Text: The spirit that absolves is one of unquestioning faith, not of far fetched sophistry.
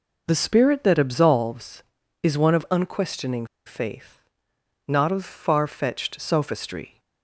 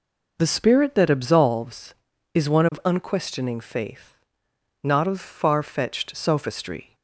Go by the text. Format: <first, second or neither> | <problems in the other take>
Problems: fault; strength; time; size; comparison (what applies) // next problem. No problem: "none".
second | pauses between "unquestioning" and "faith"; slight; at 3.4 s; 0.21 s long